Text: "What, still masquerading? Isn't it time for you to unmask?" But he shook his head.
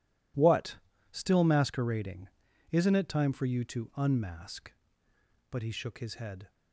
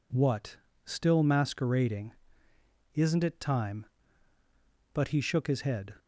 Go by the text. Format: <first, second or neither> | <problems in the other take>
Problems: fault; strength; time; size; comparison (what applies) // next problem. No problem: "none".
first | skips "for you to unmask"; at 4.3 s